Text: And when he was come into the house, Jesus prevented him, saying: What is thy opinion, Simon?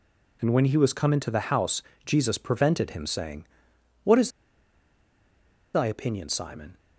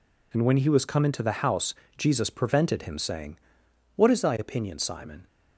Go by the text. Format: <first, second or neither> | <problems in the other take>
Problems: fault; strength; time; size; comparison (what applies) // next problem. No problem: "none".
second | pauses between "is" and "thy"; strong; at 4.2 s; 1.4 s long